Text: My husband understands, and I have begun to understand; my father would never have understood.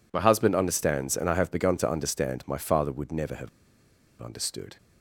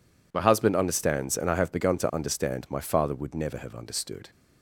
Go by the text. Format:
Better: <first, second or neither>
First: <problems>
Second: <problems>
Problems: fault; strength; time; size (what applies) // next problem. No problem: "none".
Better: second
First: pauses between "have" and "understood"; noticeable; at 3.4 s; 0.72 s long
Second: none